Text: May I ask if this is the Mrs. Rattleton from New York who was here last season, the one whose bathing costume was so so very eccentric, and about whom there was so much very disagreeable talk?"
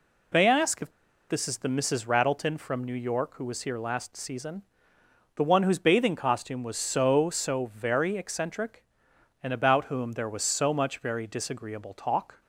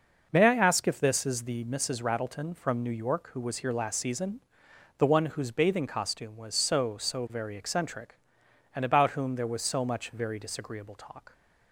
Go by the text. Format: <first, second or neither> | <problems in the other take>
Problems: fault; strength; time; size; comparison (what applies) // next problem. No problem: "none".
second | pauses between "if" and "this"; at 0.8 s; 0.40 s long